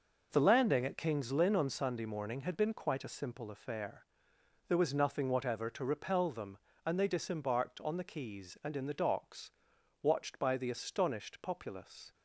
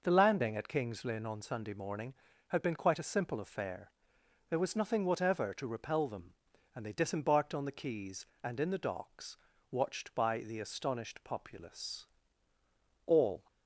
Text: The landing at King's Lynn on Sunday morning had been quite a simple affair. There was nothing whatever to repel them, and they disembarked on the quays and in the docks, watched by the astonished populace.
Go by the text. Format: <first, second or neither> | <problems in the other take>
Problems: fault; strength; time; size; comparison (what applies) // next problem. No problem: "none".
first | goes on to say "All"; slight; from 13.0 s on; 0.42 s long